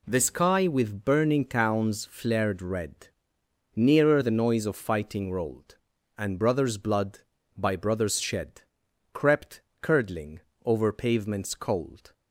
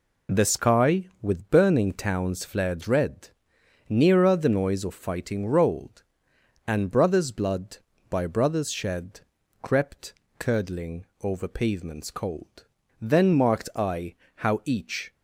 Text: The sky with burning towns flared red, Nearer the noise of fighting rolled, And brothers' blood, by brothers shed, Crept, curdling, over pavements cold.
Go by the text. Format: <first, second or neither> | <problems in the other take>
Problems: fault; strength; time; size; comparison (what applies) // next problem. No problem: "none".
first | goes on to say "Then marked I how each"; strong; from 13.0 s on; 2.1 s long